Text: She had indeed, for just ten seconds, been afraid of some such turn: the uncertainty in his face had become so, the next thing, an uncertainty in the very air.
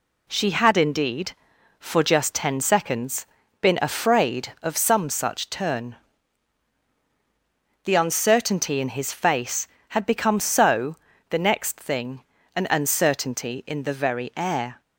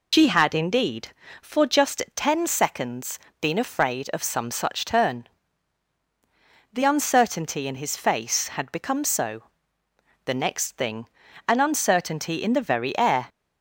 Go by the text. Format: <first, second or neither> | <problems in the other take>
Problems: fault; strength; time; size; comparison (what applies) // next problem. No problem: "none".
first | loses the start of "She"; at 0.1 s; 65 ms